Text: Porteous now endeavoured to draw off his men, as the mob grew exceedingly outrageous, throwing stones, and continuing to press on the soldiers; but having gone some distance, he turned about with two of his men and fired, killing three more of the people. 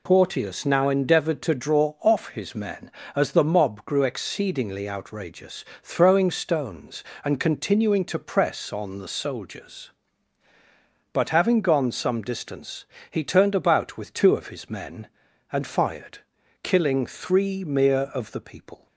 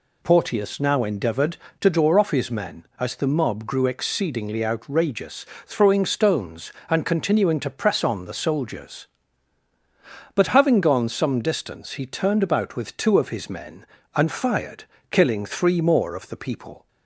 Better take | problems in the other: second | says "mere" for "more"; at 17.6 s

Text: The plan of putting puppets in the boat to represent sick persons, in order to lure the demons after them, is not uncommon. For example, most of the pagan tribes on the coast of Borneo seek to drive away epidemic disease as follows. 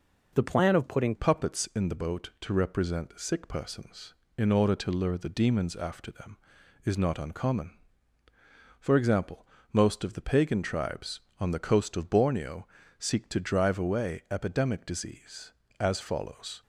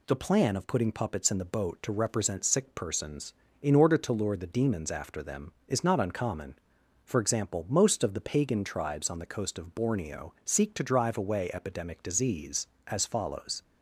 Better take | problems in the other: second | changes voice at "puppets"; from 1.1 s on; 15.5 s long // pauses between "Borneo" and "seek"; slight; at 12.6 s; 0.32 s long

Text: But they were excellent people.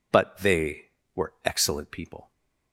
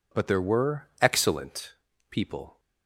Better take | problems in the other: first | says "there" for "they"; at 0.2 s // pauses between "excellent" and "people"; slight; at 1.7 s; 0.36 s long

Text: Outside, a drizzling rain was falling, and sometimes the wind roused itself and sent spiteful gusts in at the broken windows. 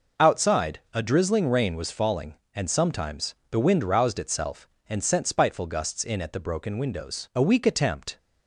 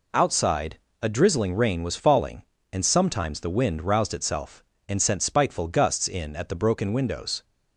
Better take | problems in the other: second | goes on to say "A weak attempt"; noticeable; from 7.3 s on; 0.82 s long

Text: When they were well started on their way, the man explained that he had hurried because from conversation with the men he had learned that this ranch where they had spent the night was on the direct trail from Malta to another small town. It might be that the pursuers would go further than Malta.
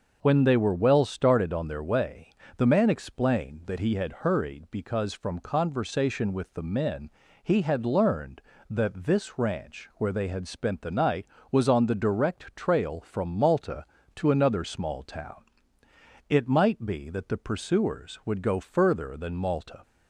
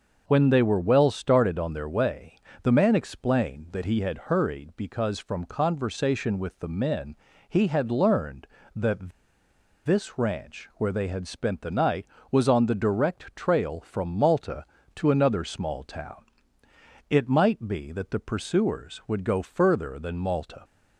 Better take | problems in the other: first | pauses between "men" and "he"; slight; at 7.1 s; 0.32 s long; slight in the first // pauses between "that" and "this"; noticeable; at 9.0 s; 0.75 s long

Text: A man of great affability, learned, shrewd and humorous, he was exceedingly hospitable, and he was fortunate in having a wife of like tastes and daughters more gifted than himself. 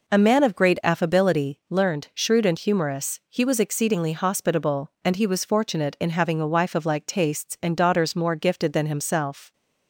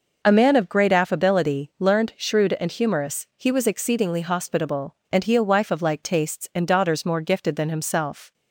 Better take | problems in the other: first | skips "was fortunate in having"; at 5.3 s

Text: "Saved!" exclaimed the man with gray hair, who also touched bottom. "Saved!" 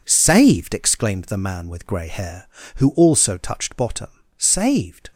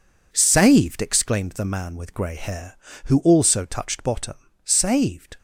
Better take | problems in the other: neither | none

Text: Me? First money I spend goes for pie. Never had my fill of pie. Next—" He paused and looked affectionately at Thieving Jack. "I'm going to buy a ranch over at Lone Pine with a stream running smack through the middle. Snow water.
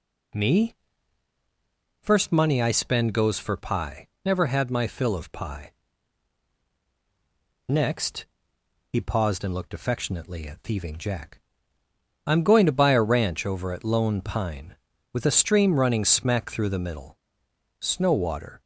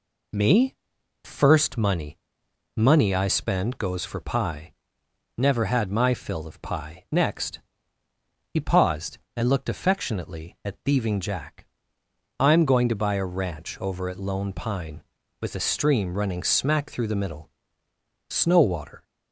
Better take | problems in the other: first | says "money" twice; at 2.7 s

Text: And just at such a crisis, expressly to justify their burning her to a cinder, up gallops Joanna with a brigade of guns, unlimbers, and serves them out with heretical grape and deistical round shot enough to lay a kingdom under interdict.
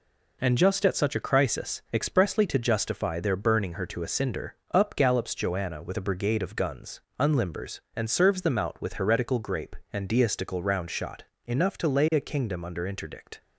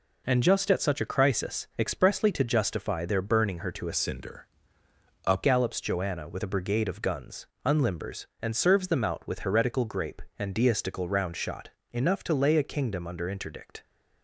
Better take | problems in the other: first | changes voice from "cinder" to "up"; from 3.9 to 5.4 s; 1.5 s long // pauses between "shot" and "enough"; slight; at 11.6 s; 0.22 s long; slight in the first

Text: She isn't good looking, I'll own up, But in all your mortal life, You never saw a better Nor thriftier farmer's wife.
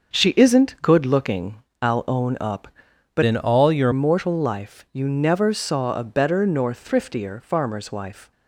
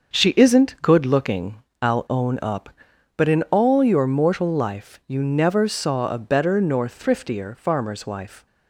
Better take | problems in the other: second | starts louder than the rest; until 1.2 s; 6.5 dB; also in the second // changes voice from "in" to "your"; from 3.2 to 3.9 s; 0.7 s long

